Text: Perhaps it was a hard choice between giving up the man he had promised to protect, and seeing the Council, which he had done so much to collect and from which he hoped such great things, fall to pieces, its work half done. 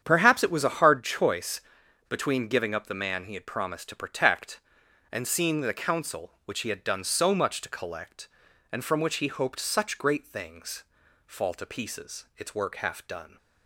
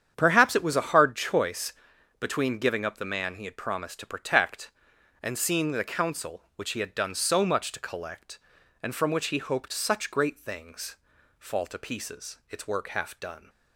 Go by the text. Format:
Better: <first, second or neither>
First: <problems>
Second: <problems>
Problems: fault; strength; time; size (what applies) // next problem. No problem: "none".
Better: neither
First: starts louder than the rest; strong; until 1.0 s; 8.5 dB // pauses between "choice" and "between"; noticeable; at 1.6 s; 0.47 s long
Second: starts louder than the rest; strong; until 1.1 s; 8.5 dB // pauses between "choice" and "between"; noticeable; at 1.7 s; 0.46 s long